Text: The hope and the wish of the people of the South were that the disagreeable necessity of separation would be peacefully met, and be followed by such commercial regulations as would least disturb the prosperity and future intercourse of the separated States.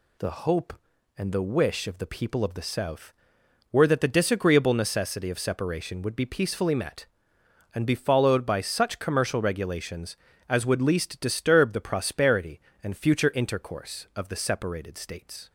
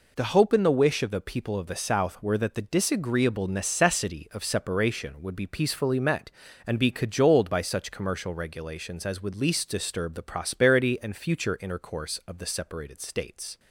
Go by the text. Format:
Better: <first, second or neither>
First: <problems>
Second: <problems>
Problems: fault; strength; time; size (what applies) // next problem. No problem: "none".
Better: first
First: none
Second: says "cajoled" for "followed"; at 6.9 s